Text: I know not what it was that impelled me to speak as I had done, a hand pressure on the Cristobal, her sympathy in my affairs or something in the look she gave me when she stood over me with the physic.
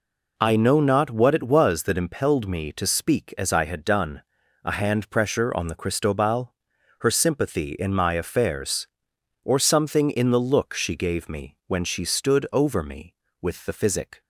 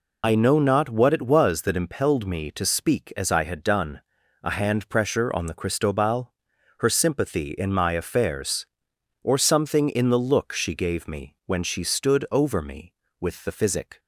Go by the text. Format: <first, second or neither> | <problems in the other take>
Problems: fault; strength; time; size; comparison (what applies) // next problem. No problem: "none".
first | loses the start of "I"; at 0.2 s; 65 ms